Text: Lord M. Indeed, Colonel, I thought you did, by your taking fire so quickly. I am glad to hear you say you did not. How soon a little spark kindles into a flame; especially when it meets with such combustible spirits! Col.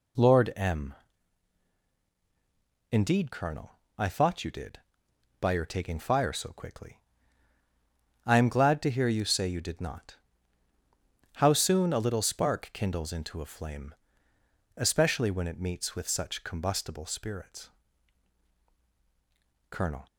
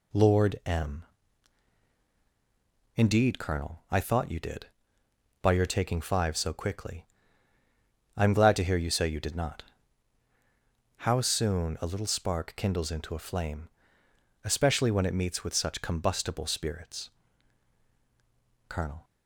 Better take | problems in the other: first | says "five" for "fire"; at 5.9 s

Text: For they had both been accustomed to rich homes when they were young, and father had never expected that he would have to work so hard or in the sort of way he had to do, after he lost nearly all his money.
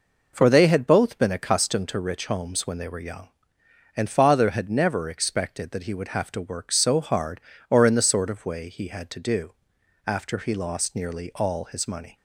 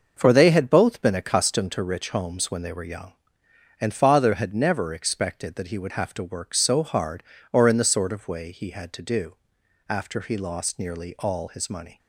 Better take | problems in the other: first | gets quieter; strong; throughout; 8 dB

